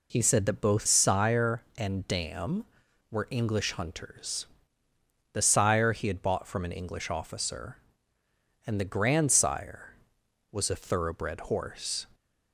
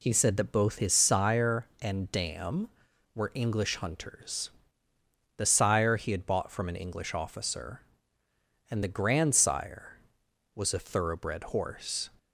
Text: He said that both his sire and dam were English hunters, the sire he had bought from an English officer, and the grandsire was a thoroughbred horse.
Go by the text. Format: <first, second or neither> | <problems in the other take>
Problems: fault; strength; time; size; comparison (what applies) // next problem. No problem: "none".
second | skips "his"; at 0.8 s